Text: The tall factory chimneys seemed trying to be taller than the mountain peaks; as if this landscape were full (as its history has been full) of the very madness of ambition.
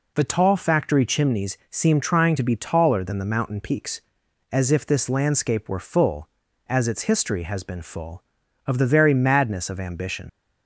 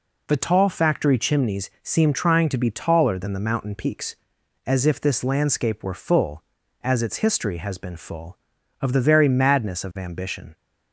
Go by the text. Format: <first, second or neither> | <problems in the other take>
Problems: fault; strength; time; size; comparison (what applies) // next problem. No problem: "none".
second | leaves "ambition" unfinished; at 10.2 s; 60 ms